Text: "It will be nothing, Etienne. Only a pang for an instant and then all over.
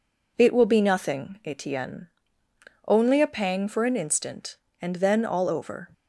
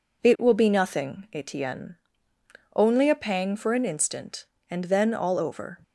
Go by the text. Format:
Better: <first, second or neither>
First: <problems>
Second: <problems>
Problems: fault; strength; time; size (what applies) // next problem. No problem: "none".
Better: neither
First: none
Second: none